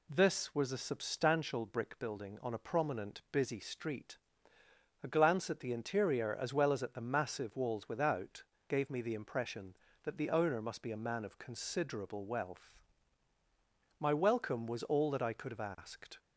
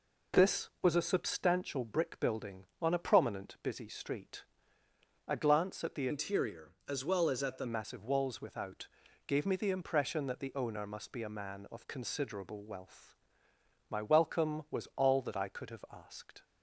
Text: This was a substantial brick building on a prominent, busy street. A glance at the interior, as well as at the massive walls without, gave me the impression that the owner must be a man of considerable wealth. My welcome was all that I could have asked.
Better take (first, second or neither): first